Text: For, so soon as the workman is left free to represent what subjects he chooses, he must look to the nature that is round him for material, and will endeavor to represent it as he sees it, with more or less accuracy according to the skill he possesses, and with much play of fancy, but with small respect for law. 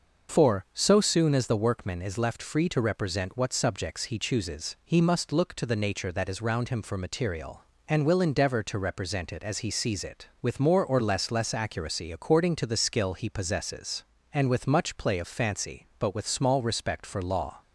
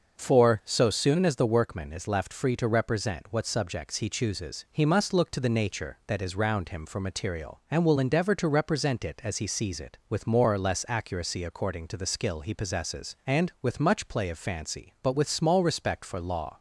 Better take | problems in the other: second | starts louder than the rest; until 1.4 s; 6 dB; also in the second // says "less" twice; at 11.3 s

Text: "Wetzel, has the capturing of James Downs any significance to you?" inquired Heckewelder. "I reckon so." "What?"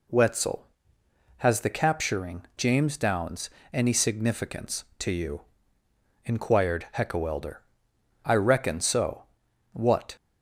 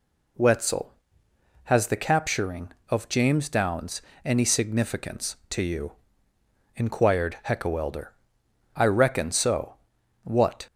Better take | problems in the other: second | skips "of"; at 2.5 s // pauses between "Downs" and "any"; slight; at 3.4 s; 0.24 s long; slight in the second

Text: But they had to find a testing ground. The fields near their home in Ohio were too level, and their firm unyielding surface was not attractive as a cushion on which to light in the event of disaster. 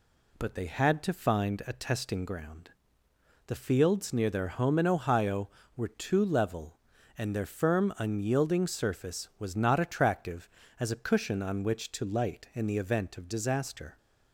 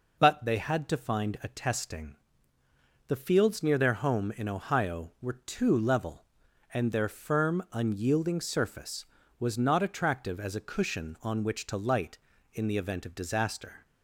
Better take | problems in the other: first | skips "ground"; at 2.6 s

